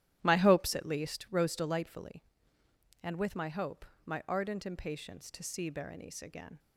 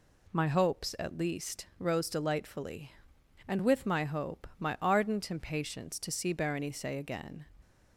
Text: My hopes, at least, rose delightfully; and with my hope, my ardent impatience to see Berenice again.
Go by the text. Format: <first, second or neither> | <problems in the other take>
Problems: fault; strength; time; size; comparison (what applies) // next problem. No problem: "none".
second | starts louder than the rest; strong; until 1.3 s; 13 dB